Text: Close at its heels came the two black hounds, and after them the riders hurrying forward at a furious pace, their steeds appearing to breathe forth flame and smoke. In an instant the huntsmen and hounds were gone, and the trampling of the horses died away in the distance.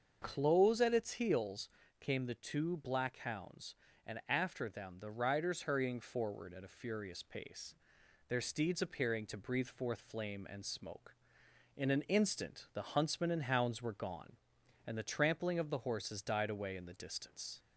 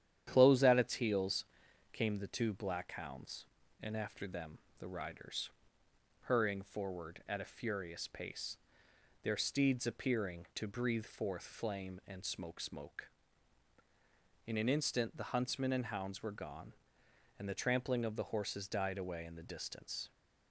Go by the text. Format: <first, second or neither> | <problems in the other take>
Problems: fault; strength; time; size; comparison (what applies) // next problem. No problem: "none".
first | starts louder than the rest; strong; until 1.3 s; 10 dB; also in the first // pauses between "heels" and "came"; noticeable; at 1.4 s; 0.46 s long; slight in the first // pauses between "them" and "the"; slight; at 4.5 s; 0.20 s long // pauses between "riders" and "hurrying"; noticeable; at 5.4 s; 0.76 s long // says "smoke" twice; at 12.6 s